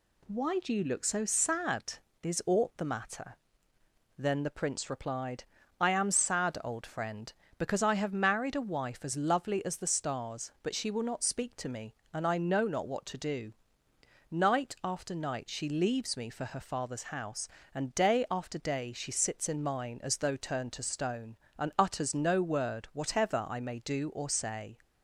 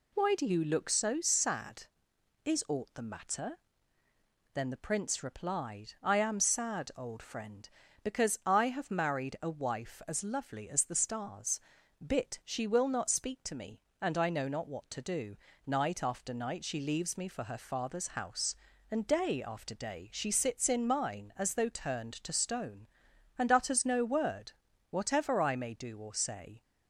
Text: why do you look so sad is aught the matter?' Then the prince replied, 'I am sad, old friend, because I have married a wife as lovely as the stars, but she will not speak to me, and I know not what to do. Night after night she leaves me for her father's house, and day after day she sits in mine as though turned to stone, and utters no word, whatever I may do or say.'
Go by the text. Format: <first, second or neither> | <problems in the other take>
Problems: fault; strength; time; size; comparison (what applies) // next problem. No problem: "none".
first | says "bit" for "but"; at 12.0 s